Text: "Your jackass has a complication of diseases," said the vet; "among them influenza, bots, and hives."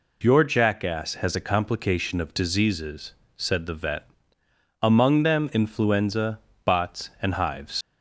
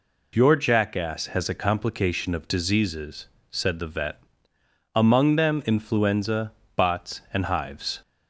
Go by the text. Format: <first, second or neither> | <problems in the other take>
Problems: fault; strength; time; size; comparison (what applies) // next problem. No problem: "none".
second | leaves "hives" unfinished; at 7.8 s; 90 ms